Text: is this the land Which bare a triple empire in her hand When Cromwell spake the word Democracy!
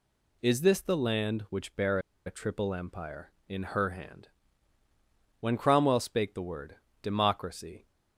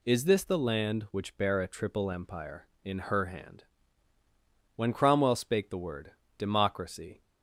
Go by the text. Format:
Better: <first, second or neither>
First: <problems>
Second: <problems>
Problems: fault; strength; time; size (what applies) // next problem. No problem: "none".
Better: second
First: pauses between "bare" and "a"; slight; at 1.9 s; 0.27 s long // pauses between "hand" and "When"; at 4.2 s; 1.1 s long // pauses between "word" and "Democracy"; slight; at 6.7 s; 0.26 s long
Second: pauses between "hand" and "When"; at 3.6 s; 1.1 s long // pauses between "word" and "Democracy"; slight; at 6.1 s; 0.26 s long